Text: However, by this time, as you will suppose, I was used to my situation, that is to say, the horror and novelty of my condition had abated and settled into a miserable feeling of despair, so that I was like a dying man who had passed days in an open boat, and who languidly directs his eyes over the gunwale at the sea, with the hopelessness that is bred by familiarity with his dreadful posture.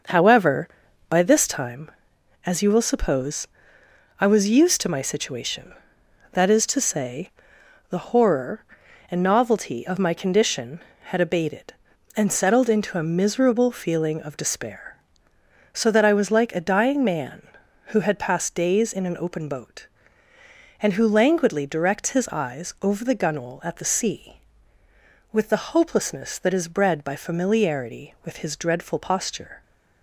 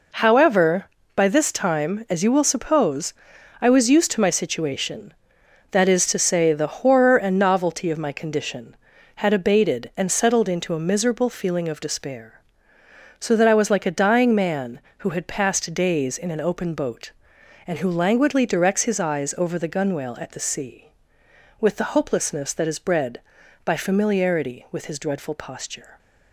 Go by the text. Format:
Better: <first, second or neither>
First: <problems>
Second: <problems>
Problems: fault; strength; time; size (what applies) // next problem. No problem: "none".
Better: second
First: starts louder than the rest; until 1.7 s; 6.5 dB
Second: none